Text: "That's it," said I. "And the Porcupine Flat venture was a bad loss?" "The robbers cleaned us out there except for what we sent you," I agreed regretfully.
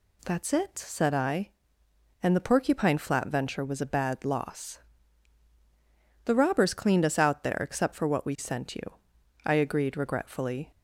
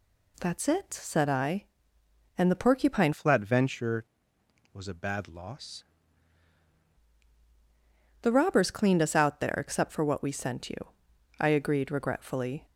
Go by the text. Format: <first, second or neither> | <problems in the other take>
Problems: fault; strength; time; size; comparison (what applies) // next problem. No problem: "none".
first | changes voice from "Flat" to "loss"; from 3.1 to 5.8 s; 2.7 s long